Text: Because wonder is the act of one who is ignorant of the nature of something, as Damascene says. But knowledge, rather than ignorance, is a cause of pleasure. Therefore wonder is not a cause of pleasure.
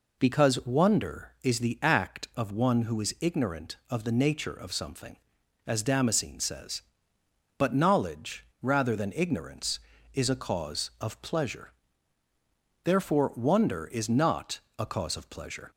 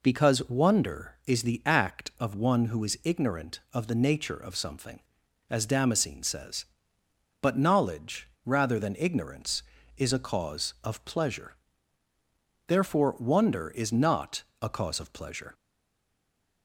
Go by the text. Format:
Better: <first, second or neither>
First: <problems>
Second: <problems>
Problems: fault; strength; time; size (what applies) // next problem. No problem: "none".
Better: first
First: pauses between "not" and "a"; slight; at 14.5 s; 0.18 s long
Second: pauses between "not" and "a"; slight; at 14.4 s; 0.18 s long // stays silent after the last word; from 15.5 s on; 1.1 s long